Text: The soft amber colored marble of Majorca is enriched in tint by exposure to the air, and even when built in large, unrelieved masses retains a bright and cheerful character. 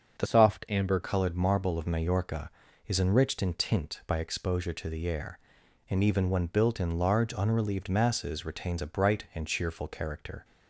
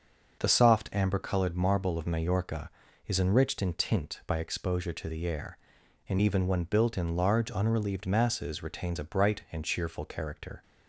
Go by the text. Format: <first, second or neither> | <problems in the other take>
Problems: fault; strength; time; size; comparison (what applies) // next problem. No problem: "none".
second | starts louder than the rest; until 1.2 s; 6.5 dB; also in the second // changes voice from "soft" to "amber"; from 0.2 to 0.9 s; 0.7 s long